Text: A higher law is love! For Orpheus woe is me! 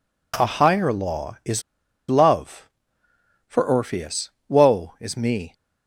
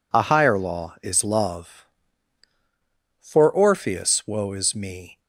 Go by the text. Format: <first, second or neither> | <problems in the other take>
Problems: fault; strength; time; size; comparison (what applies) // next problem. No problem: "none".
second | pauses between "is" and "love"; noticeable; at 1.6 s; 0.47 s long // pauses between "Orpheus" and "woe"; slight; at 4.3 s; 0.18 s long